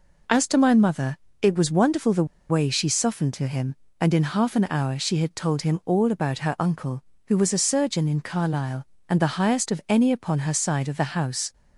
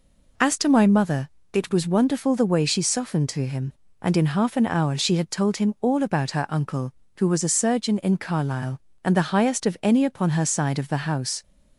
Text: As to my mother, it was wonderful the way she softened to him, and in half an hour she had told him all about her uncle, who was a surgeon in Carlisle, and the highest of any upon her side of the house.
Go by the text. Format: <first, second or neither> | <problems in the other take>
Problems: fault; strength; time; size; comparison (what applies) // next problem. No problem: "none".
second | pauses between "the" and "way"; slight; at 2.2 s; 0.25 s long